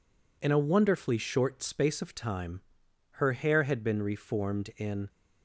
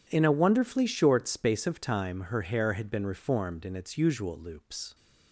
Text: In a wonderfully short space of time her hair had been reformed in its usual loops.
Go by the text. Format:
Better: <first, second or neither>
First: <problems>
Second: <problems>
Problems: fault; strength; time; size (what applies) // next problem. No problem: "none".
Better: second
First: pauses between "time" and "her"; noticeable; at 2.6 s; 0.52 s long // stops before "its usual loops"; at 5.0 s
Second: none